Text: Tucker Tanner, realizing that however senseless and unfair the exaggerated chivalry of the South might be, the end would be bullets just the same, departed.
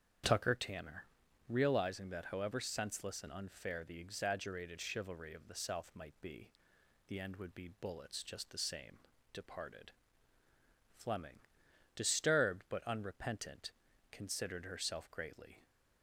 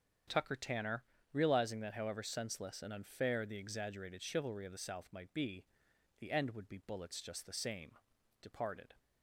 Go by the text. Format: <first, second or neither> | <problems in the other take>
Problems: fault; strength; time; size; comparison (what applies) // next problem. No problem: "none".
second | starts louder than the rest; strong; until 1.6 s; 8 dB; strong in the second // goes on to say "Fleming disturbed but unrepentant considered herself greatly"; strong; from 10.9 s on; 4.7 s long